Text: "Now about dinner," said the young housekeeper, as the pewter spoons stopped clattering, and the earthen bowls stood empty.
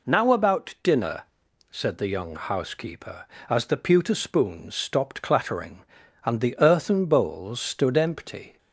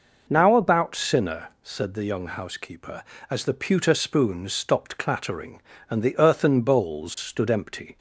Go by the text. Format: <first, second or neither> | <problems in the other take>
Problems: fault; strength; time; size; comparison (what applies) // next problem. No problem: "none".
first | says "sinner" for "dinner"; at 0.9 s